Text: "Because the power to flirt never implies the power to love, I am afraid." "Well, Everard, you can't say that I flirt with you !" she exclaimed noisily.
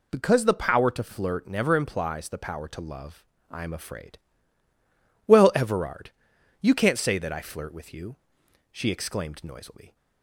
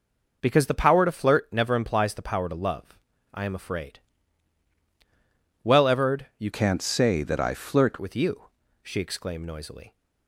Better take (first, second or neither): first